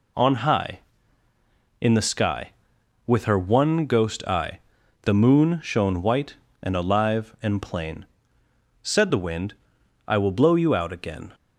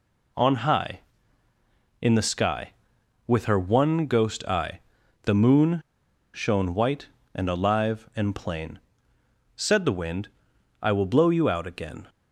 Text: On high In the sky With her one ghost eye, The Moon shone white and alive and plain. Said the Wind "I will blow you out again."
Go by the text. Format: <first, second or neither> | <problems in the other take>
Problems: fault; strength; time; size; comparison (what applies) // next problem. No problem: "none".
first | pauses between "Moon" and "shone"; noticeable; at 5.8 s; 0.55 s long // pauses between "Wind" and "I"; noticeable; at 10.2 s; 0.56 s long; noticeable in the first